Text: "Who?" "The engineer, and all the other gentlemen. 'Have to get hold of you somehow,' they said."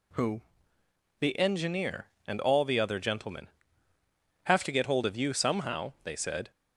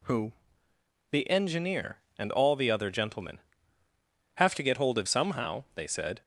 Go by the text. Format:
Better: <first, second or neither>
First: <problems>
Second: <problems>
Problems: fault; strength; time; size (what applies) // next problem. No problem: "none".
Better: first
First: none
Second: skips "you"; at 5.0 s